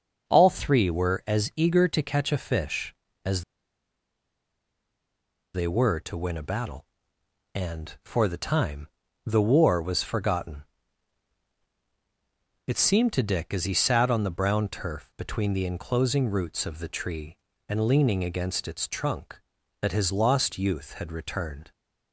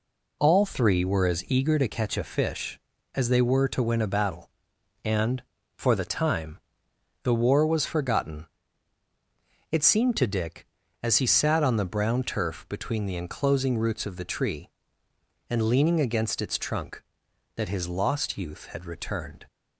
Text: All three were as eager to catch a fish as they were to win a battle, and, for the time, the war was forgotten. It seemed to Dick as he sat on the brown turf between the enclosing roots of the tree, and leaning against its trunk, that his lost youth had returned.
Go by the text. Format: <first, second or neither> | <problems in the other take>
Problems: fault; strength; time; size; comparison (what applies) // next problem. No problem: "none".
second | starts louder than the rest; until 1.3 s; 6 dB // pauses between "as" and "they"; strong; at 3.4 s; 2.1 s long